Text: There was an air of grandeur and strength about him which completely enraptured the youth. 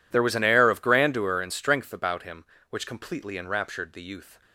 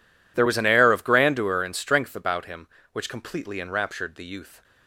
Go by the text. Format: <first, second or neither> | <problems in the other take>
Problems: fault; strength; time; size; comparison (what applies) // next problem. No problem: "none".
neither | none